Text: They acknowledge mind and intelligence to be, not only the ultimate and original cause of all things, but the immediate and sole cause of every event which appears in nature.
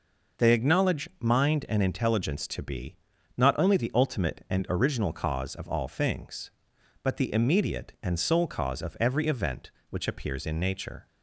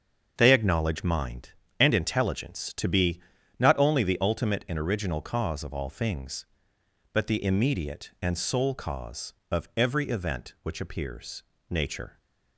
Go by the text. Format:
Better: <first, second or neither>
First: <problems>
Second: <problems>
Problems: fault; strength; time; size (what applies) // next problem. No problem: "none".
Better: first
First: none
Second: starts louder than the rest; until 1.3 s; 7 dB // skips "in"; at 11.5 s